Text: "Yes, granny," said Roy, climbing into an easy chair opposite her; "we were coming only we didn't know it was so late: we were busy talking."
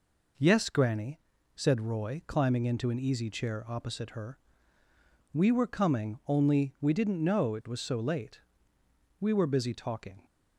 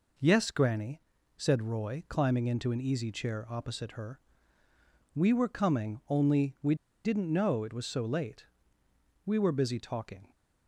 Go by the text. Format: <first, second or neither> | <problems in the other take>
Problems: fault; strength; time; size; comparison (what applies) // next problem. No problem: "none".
first | pauses between "we" and "didn't"; slight; at 6.7 s; 0.30 s long